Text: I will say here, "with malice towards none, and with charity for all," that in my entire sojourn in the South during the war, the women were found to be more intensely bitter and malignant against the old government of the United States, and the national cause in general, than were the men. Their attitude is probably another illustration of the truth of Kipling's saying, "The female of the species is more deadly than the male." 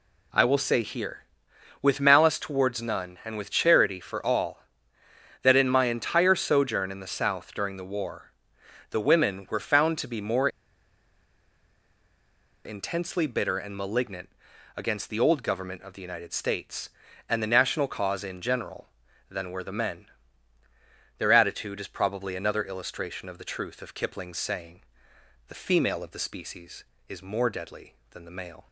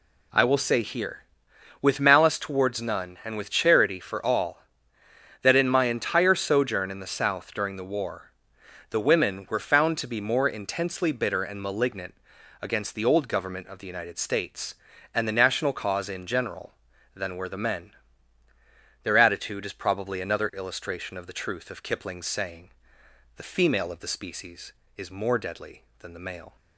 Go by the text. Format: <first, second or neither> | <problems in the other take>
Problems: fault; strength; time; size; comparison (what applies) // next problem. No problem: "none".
second | pauses between "more" and "intensely"; strong; at 10.4 s; 2.1 s long // pauses between "malignant" and "against"; noticeable; at 14.2 s; 0.48 s long; noticeable in the second